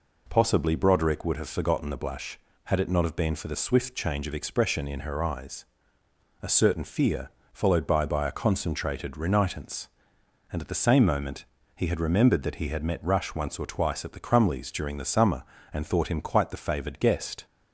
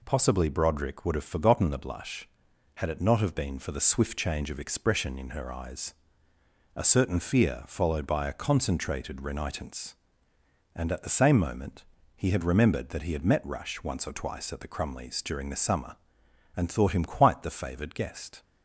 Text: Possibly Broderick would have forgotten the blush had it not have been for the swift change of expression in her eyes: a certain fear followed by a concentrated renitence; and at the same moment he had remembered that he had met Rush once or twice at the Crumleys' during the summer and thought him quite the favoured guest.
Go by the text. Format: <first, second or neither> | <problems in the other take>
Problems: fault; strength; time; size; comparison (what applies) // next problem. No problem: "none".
second | pauses between "fear" and "followed"; slight; at 7.2 s; 0.24 s long // says "by" twice; at 8.0 s // pauses between "moment" and "he"; slight; at 11.4 s; 0.32 s long; slight in the second